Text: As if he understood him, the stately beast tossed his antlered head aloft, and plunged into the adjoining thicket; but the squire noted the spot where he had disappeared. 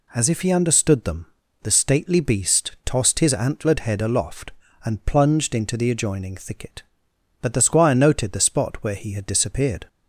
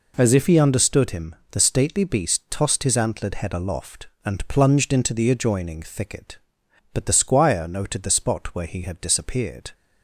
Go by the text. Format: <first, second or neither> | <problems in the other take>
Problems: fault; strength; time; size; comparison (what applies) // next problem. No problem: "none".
second | says "them" for "him"; at 1.0 s